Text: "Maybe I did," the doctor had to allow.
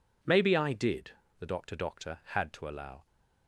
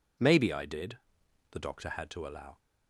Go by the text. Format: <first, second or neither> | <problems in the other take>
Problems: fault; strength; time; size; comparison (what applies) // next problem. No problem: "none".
second | says "doctor" twice; at 1.7 s